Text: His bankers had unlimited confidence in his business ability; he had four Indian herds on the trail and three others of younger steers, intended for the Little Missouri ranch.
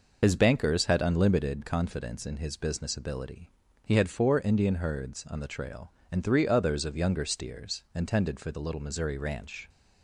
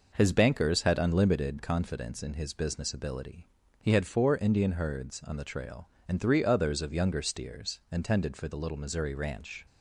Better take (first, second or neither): second